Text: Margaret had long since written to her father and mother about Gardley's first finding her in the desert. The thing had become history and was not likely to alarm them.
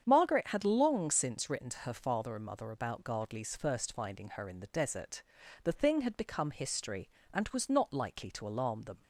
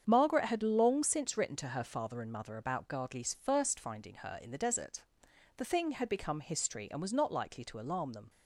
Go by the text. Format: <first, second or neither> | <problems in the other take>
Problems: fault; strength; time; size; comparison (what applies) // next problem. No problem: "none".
neither | starts louder than the rest; strong; the same in both